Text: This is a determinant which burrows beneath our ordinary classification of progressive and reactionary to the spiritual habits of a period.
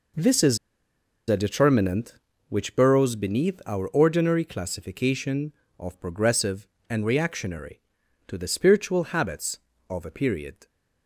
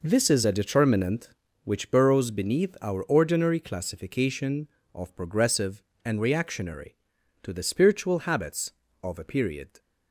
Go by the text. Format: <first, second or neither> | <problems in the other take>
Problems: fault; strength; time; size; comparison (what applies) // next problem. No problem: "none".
second | pauses between "is" and "a"; noticeable; at 0.5 s; 0.72 s long